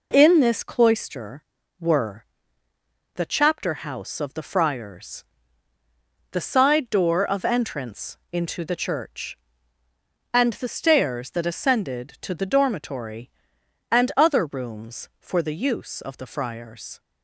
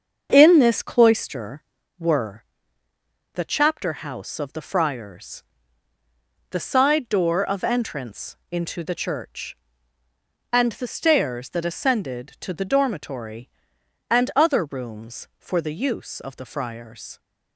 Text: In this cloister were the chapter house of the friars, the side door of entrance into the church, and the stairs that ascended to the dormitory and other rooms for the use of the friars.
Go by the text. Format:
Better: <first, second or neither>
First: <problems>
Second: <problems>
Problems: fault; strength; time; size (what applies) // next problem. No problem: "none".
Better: first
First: pauses between "were" and "the"; noticeable; at 2.2 s; 0.88 s long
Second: starts louder than the rest; until 2.0 s; 7 dB // pauses between "were" and "the"; noticeable; at 2.4 s; 0.88 s long